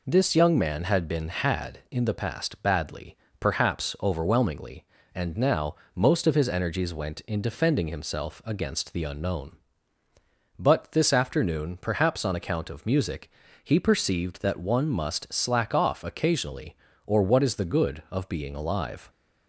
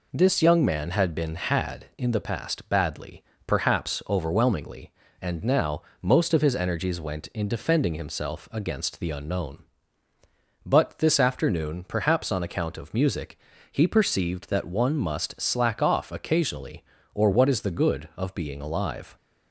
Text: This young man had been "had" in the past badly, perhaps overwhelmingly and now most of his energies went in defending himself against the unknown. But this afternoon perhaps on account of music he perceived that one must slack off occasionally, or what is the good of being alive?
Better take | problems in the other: neither | pauses between "now" and "most"; slight; the same in both // pauses between "music" and "he"; slight; the same in both

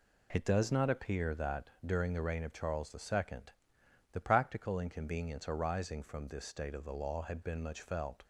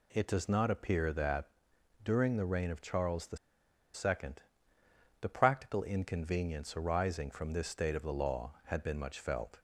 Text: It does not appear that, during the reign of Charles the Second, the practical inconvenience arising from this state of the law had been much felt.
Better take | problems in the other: first | pauses between "the" and "Second"; noticeable; at 3.3 s; 0.56 s long

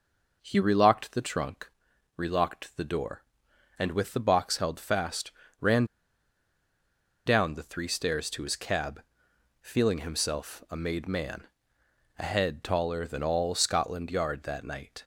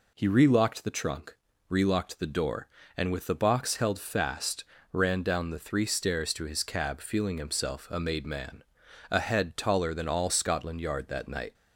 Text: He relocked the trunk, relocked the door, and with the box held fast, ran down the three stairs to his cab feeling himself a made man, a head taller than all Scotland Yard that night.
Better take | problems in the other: second | pauses between "ran" and "down"; strong; at 5.8 s; 1.4 s long // pauses between "cab" and "feeling"; noticeable; at 9.0 s; 0.60 s long

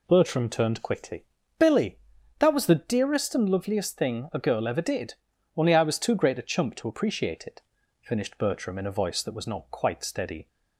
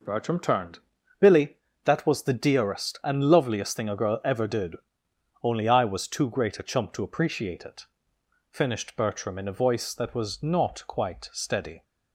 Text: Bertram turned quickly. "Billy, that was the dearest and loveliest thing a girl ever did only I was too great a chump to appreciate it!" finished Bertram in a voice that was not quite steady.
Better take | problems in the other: first | skips "quickly"; at 0.9 s // pauses between "did" and "only"; noticeable; at 4.7 s; 0.68 s long; also in the first

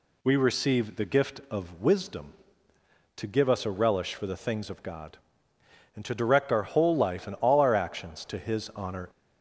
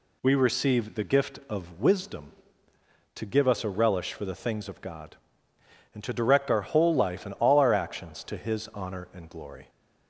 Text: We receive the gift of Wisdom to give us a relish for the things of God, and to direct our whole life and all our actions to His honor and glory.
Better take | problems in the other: second | stops before "and glory"; at 9.1 s

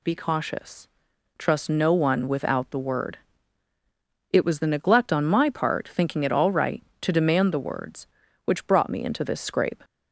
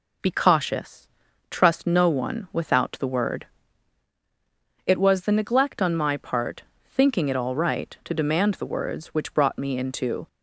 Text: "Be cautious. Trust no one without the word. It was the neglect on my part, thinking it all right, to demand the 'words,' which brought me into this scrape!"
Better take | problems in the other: first | stops before "this scrape"; at 10.2 s

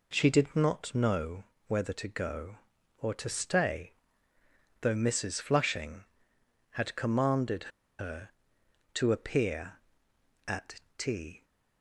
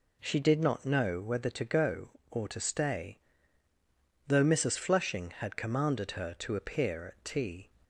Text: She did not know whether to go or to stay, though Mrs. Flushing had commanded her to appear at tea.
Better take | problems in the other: second | pauses between "know" and "whether"; slight; at 1.4 s; 0.24 s long // pauses between "commanded" and "her"; slight; at 7.7 s; 0.29 s long // pauses between "at" and "tea"; slight; at 10.7 s; 0.16 s long

